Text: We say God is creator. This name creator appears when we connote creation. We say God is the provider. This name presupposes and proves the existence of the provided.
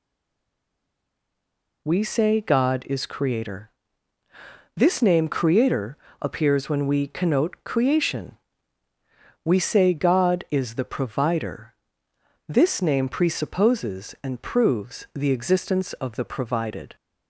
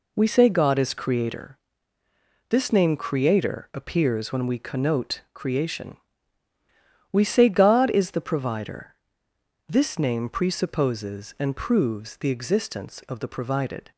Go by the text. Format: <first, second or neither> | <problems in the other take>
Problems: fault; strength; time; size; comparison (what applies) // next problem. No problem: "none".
second | stays silent before the first word; noticeable; until 1.8 s; 1.8 s long // pauses between "creator" and "appears"; slight; at 5.9 s; 0.24 s long